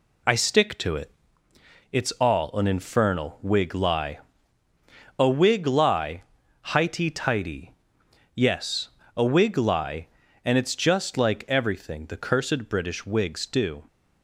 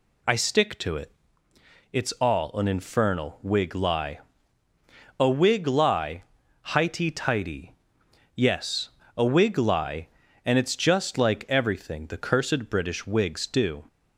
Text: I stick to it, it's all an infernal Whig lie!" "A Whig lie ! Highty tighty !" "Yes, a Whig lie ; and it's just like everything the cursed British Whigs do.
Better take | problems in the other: second | gets quieter; noticeable; throughout; 5 dB

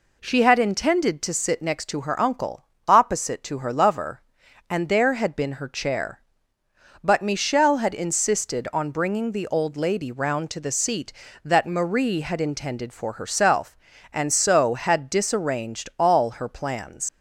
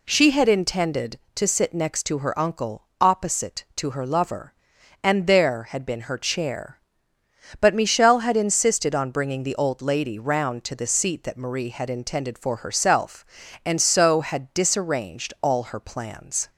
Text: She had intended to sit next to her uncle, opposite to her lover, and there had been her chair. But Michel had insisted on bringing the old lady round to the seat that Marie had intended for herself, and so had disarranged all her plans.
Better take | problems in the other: second | leaves "plans" unfinished; at 17.0 s; 100 ms

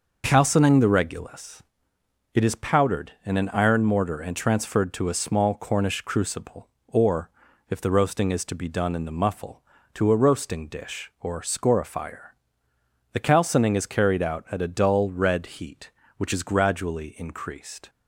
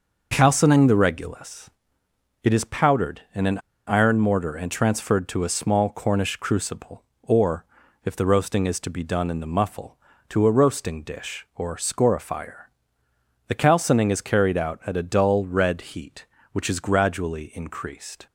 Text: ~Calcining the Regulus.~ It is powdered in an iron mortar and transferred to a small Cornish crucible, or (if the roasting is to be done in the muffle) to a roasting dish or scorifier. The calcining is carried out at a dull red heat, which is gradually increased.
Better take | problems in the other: first | starts louder than the rest; noticeable; until 1.3 s; 6 dB; noticeable in the first // pauses between "an" and "iron"; slight; at 3.5 s; 0.28 s long

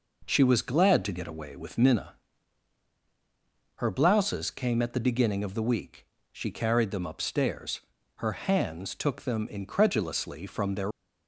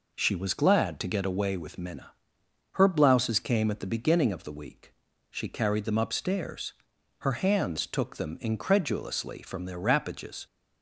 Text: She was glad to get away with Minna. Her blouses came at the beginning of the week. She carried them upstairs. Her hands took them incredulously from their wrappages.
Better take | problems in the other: second | stops before "wrappages"; at 10.9 s

